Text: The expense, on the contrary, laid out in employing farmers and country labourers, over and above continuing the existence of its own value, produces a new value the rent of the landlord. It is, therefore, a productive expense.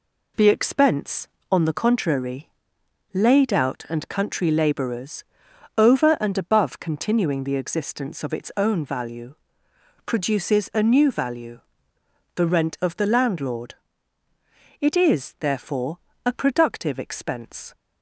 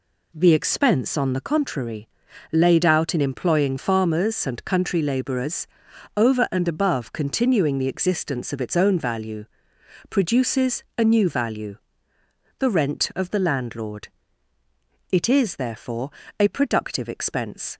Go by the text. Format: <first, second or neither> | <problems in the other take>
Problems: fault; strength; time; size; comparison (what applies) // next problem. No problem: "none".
second | skips "in employing farmers"; at 3.8 s // pauses between "value" and "the"; noticeable; at 11.5 s; 0.74 s long; noticeable in the second